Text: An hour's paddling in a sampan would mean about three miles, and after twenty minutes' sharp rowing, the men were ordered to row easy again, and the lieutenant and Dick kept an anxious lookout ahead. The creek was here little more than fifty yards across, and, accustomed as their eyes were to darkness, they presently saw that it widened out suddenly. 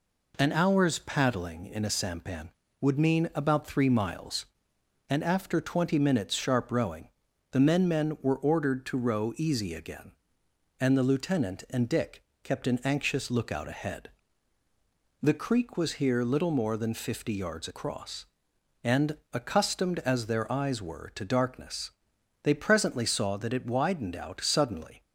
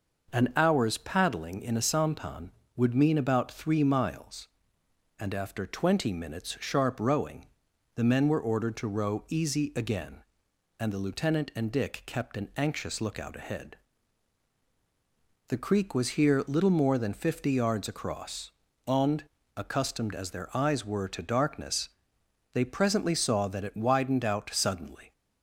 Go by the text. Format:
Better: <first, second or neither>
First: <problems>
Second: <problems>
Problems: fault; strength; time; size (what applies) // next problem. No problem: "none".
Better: second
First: says "men" twice; at 7.8 s // pauses between "Dick" and "kept"; slight; at 12.2 s; 0.22 s long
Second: none